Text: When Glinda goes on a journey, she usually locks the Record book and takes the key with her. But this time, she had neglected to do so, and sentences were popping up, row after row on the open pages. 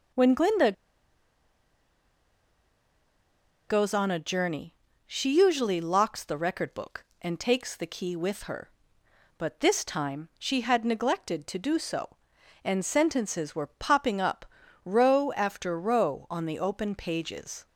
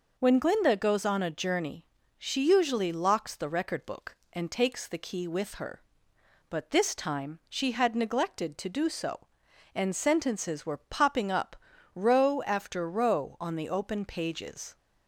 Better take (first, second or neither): second